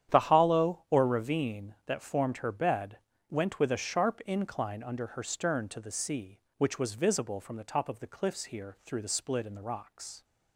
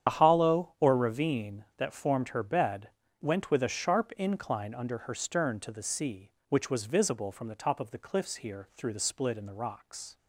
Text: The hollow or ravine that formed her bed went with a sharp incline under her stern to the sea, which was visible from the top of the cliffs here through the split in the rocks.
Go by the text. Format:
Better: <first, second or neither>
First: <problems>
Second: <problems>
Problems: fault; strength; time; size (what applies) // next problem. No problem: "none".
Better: first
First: starts louder than the rest; strong; until 1.1 s; 9.5 dB // pauses between "bed" and "went"; slight; at 2.9 s; 0.32 s long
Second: loses the start of "The"; at 0.0 s; 80 ms // starts louder than the rest; strong; until 1.1 s; 9 dB // pauses between "bed" and "went"; slight; at 2.8 s; 0.32 s long